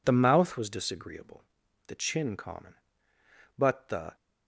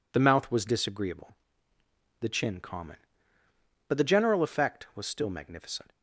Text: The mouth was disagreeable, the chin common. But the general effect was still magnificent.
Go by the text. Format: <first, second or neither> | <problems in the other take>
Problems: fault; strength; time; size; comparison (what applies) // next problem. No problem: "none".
second | stops before "general effect was still magnificent"; at 4.1 s